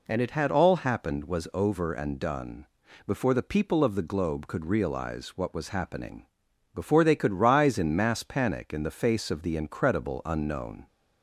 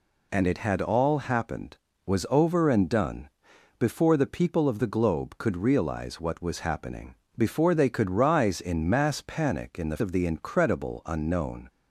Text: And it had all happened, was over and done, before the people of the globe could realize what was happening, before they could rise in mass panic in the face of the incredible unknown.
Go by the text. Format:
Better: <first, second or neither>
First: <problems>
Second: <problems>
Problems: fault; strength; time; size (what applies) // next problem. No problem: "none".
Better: first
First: none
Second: skips "face"; at 9.9 s